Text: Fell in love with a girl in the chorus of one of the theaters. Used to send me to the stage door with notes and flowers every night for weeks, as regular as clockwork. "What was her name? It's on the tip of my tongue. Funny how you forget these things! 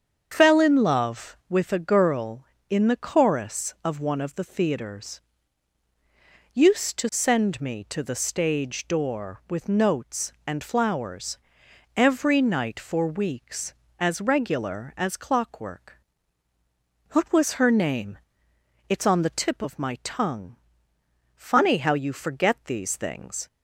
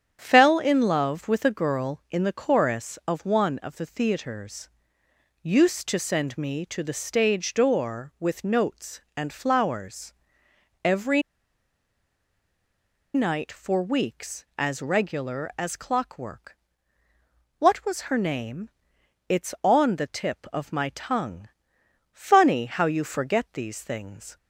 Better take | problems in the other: first | starts louder than the rest; strong; until 1.2 s; 9 dB; strong in the first // pauses between "flowers" and "every"; noticeable; at 10.1 s; 0.72 s long; noticeable in the first // pauses between "every" and "night"; strong; at 11.2 s; 1.9 s long

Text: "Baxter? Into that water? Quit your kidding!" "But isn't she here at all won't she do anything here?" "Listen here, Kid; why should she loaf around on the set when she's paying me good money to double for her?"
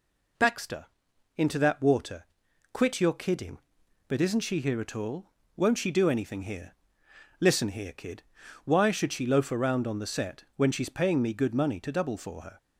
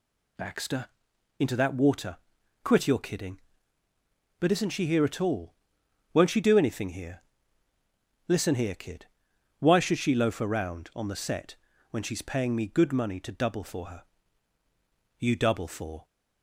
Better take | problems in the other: first | pauses between "all" and "won't"; noticeable; at 5.5 s; 0.58 s long; slight in the first // pauses between "set" and "when"; slight; at 11.5 s; 0.34 s long // goes on to say "You double for"; noticeable; from 15.1 s on; 0.88 s long

